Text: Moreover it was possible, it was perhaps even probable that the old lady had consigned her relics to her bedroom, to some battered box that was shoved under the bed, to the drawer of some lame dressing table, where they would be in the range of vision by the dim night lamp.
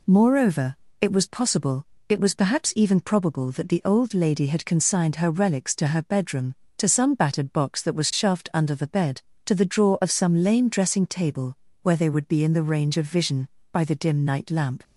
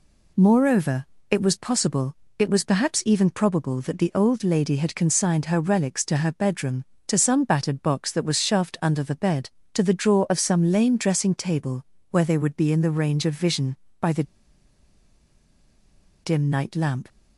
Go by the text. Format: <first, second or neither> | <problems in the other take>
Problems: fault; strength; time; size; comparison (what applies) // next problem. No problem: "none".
first | pauses between "Moreover" and "it"; slight; at 1.0 s; 0.24 s long; slight in the first // pauses between "the" and "dim"; strong; at 14.2 s; 2.0 s long